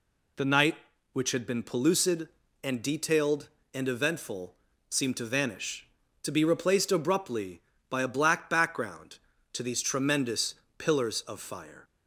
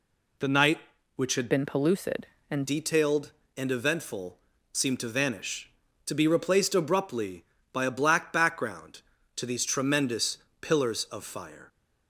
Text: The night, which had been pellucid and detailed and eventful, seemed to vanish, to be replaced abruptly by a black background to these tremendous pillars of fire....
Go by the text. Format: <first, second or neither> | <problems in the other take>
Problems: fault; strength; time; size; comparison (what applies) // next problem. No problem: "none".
first | changes voice from "been" to "and"; from 1.4 to 2.6 s; 1.2 s long // pauses between "tremendous" and "pillars"; slight; at 10.3 s; 0.22 s long; slight in the first